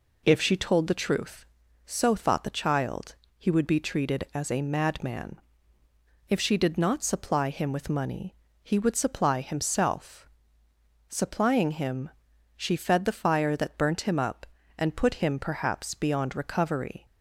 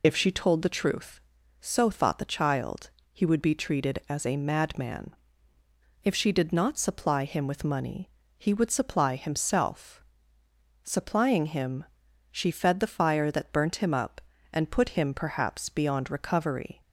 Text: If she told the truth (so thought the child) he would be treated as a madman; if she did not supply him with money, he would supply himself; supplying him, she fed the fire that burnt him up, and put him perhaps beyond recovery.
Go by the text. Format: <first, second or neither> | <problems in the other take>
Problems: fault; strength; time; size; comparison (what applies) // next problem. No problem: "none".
first | loses the start of "If"; at 0.0 s; 45 ms